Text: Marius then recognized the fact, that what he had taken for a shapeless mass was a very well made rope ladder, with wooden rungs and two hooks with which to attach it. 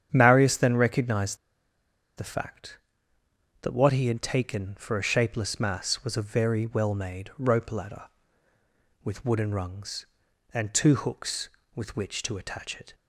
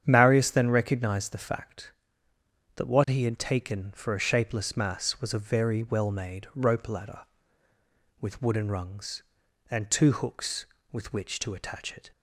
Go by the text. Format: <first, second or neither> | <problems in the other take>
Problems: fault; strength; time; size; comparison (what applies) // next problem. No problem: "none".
second | starts louder than the rest; strong; until 1.1 s; 8.5 dB; strong in the second // pauses between "recognized" and "the"; noticeable; at 1.3 s; 0.81 s long